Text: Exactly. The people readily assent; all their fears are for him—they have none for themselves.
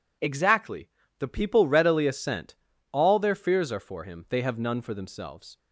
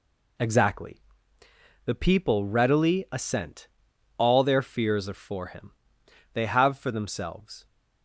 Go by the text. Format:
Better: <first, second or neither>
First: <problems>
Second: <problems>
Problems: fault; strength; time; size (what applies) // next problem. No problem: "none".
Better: first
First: none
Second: skips "none"; at 6.7 s